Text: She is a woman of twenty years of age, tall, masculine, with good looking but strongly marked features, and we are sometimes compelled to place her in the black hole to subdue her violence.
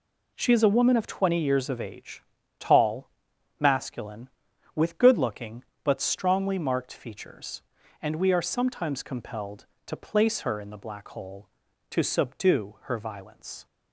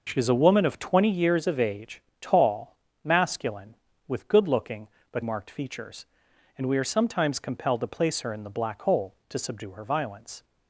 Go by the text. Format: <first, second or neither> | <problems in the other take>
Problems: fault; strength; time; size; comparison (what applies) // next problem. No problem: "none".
first | skips "strongly"; at 5.2 s